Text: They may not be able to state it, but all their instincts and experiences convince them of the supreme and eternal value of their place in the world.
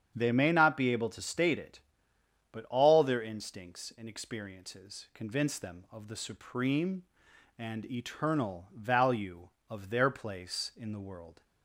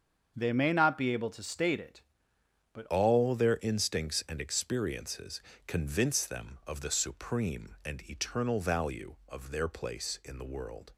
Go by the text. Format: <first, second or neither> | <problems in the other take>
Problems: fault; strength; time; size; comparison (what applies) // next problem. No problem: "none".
first | starts louder than the rest; until 1.3 s; 6.5 dB; strong in the first // changes voice at "all"; from 2.8 s on; 8.1 s long // pauses between "experiences" and "convince"; slight; at 5.4 s; 0.26 s long